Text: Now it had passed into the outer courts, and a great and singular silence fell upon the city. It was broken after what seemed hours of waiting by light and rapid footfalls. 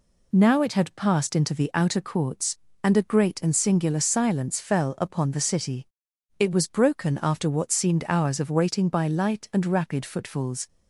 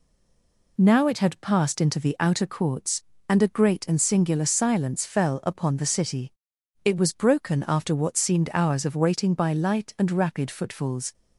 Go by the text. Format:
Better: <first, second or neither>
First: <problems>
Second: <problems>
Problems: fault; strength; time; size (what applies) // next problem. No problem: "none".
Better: first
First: none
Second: stays silent before the first word; slight; until 0.7 s; 0.7 s long